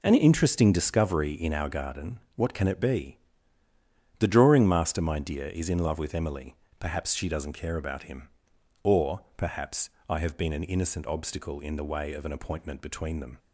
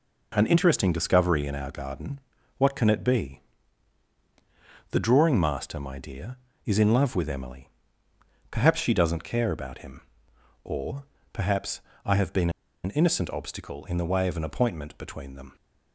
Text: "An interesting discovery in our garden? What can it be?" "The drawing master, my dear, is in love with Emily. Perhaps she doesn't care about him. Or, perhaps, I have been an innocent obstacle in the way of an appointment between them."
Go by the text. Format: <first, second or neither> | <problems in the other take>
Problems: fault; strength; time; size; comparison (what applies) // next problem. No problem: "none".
first | pauses between "been" and "an"; slight; at 12.4 s; 0.34 s long